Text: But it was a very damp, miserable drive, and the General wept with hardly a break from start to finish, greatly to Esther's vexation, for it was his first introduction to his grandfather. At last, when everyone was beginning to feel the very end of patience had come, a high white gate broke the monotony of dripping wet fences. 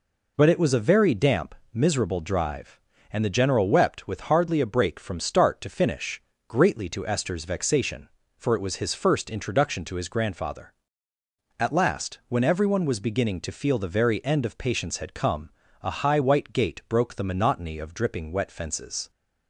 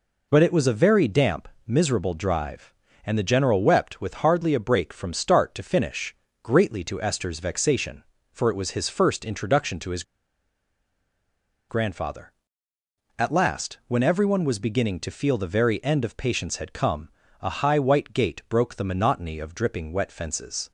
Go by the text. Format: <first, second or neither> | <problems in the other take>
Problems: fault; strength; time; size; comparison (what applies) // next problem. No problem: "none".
first | pauses between "his" and "grandfather"; strong; at 10.0 s; 1.6 s long